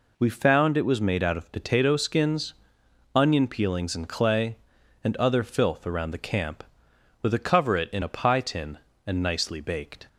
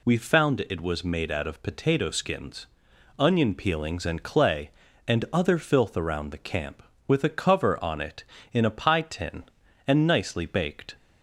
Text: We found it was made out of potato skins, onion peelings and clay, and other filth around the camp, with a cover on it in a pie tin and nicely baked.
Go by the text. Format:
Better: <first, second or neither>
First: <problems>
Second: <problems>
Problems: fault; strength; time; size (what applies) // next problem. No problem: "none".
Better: second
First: skips "on"; at 7.7 s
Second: none